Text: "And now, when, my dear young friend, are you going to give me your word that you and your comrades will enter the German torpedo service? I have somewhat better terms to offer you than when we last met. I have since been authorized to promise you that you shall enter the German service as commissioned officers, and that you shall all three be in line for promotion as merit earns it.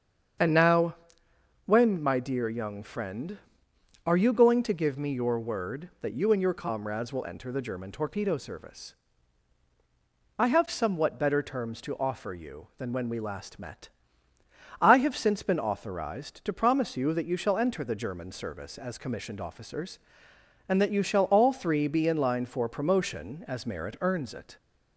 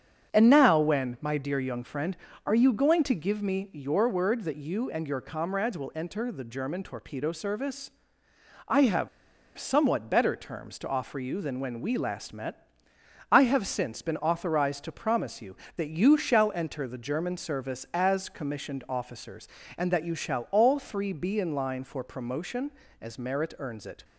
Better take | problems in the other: first | starts louder than the rest; strong; until 1.3 s; 7.5 dB; strong in the first // pauses between "have" and "somewhat"; noticeable; at 9.0 s; 0.49 s long

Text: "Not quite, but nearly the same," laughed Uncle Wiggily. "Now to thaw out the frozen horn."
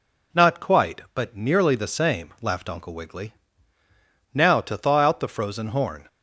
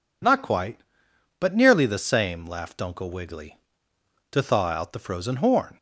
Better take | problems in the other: first | skips "Now"; at 3.9 s

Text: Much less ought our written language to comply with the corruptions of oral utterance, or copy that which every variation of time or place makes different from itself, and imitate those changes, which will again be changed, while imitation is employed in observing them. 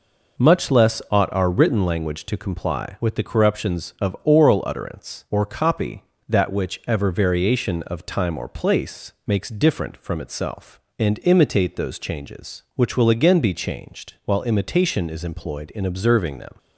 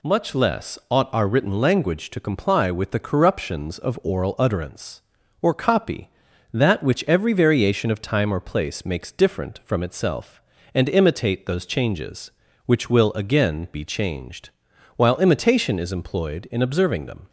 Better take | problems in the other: second | says "ever" for "every"; at 6.8 s

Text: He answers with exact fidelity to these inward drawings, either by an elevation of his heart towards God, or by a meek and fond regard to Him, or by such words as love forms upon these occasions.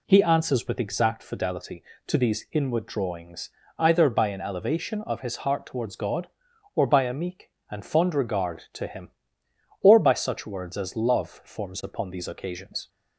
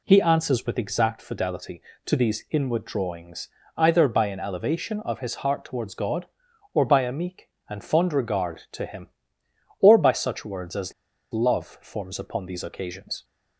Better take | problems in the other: first | pauses between "as" and "love"; at 10.9 s; 0.41 s long

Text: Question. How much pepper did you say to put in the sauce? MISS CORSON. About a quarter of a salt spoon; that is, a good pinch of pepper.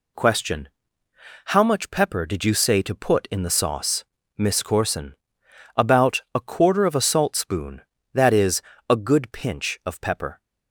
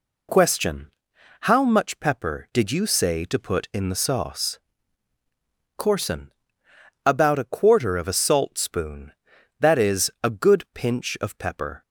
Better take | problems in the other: first | skips "MISS"; at 5.1 s

